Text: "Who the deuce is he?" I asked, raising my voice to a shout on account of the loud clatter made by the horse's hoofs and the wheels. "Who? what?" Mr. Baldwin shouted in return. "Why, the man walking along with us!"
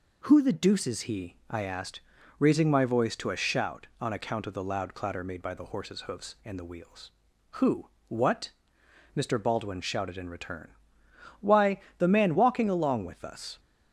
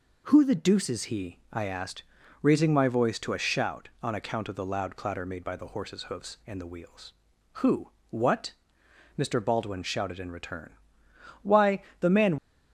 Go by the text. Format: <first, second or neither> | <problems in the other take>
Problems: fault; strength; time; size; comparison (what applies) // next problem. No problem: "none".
first | stops before "walking along with us"; at 12.3 s